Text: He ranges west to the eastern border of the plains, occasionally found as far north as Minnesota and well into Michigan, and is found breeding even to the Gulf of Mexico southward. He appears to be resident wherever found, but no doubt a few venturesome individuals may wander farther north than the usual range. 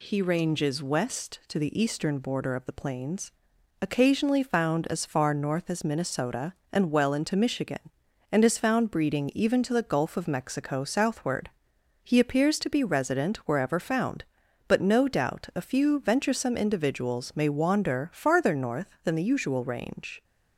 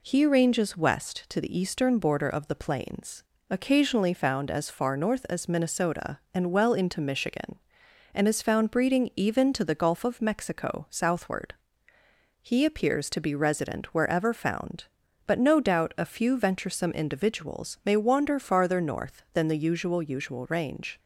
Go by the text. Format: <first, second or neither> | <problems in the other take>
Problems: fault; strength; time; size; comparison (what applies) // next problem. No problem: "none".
first | says "usual" twice; at 20.0 s